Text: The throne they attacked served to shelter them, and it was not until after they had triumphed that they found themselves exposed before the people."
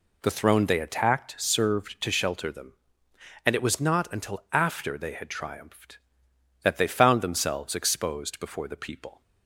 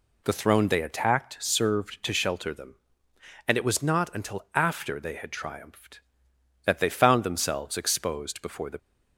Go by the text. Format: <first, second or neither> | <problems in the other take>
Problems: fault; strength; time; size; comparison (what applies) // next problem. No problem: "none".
first | stops before "people"; at 8.7 s